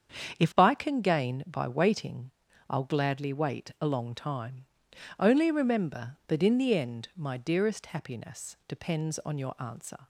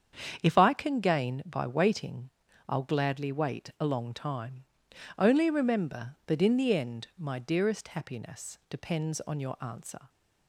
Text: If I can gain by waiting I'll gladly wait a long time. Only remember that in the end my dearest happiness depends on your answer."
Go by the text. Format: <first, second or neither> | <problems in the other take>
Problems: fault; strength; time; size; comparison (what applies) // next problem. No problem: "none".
neither | starts louder than the rest; strong; the same in both // pauses between "waiting" and "I'll"; the same in both